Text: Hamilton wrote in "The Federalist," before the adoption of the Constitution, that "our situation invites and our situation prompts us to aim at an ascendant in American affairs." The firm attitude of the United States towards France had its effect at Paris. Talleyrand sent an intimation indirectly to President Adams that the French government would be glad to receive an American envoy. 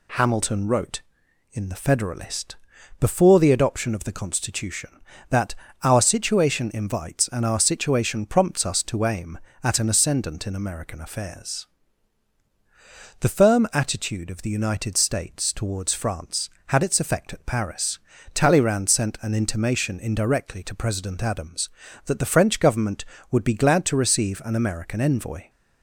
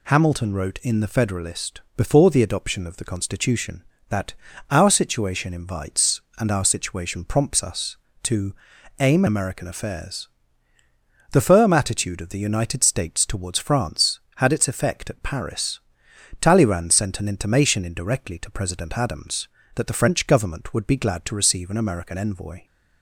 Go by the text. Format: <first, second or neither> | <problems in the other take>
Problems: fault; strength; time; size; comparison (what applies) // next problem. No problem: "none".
first | pauses between "that" and "our"; slight; at 4.3 s; 0.36 s long; slight in the first // pauses between "to" and "aim"; noticeable; at 8.5 s; 0.46 s long // skips "at an ascendant in"; at 9.2 s